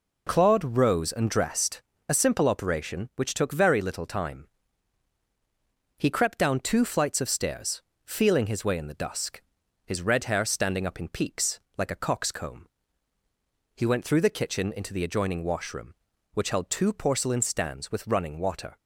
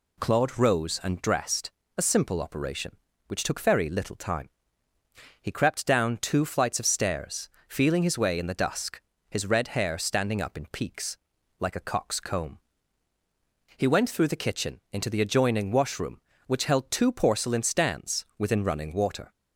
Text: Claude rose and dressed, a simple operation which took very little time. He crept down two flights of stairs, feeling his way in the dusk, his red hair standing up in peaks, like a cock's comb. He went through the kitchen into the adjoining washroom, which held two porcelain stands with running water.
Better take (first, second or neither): first